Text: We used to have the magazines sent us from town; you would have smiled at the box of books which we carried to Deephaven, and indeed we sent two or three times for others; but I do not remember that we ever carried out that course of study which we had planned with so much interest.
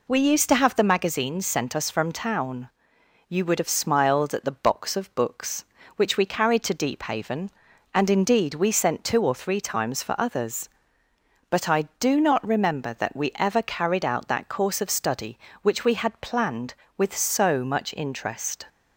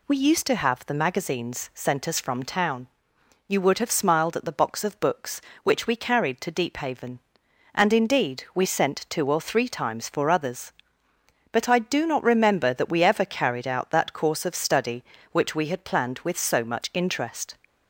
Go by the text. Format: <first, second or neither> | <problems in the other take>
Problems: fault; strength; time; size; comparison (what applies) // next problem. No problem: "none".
neither | none